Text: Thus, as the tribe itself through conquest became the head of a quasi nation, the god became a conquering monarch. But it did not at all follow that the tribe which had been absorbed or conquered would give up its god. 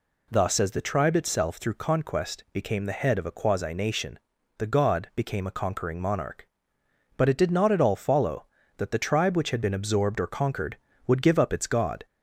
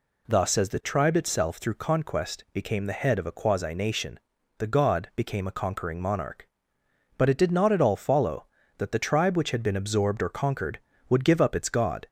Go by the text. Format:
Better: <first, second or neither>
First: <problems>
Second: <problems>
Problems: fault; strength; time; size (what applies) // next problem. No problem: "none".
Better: neither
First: none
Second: none